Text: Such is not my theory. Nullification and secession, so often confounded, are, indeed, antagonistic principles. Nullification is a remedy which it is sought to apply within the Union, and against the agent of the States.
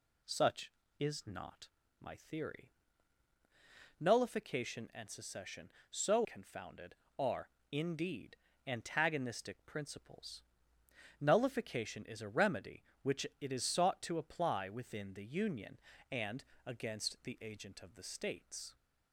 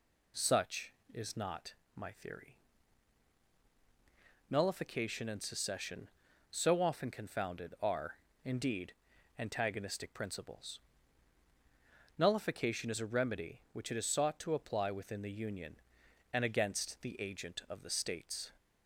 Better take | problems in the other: second | pauses between "not" and "my"; slight; at 1.6 s; 0.32 s long; slight in the second // skips "often"; at 6.2 s // pauses between "and" and "against"; slight; at 16.4 s; 0.22 s long

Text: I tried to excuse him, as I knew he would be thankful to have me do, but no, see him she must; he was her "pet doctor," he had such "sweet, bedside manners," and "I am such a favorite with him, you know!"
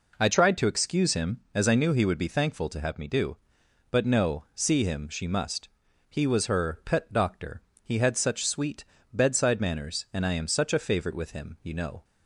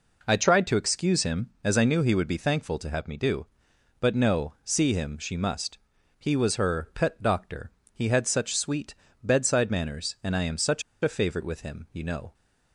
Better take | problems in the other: first | pauses between "such" and "a"; slight; at 10.8 s; 0.21 s long

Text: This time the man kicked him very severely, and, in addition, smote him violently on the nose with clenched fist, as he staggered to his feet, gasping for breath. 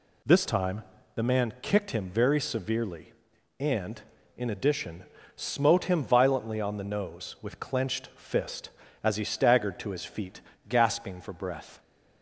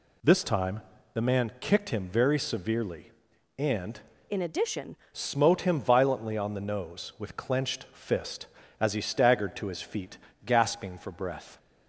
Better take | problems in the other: first | pauses between "time" and "the"; slight; at 0.8 s; 0.32 s long; slight in the first // changes voice from "in" to "addition"; from 4.2 to 4.9 s; 0.7 s long

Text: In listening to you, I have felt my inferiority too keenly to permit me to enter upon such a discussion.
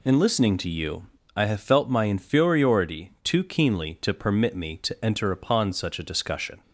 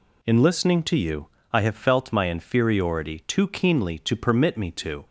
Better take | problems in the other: first | stops before "enter upon such a discussion"; at 5.0 s

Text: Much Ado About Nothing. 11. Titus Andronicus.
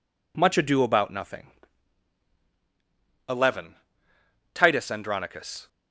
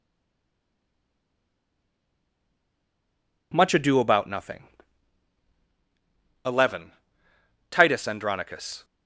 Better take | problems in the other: first | stays silent before the first word; strong; until 3.5 s; 3.5 s long

